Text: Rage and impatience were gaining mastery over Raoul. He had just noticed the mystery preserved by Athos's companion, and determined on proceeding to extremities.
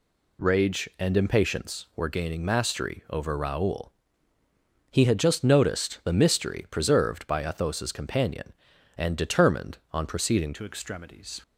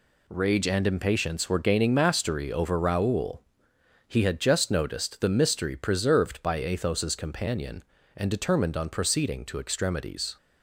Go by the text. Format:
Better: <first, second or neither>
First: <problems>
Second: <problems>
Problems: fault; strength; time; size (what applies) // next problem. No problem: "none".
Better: second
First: changes voice at "to"; from 10.5 s on; 0.9 s long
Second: none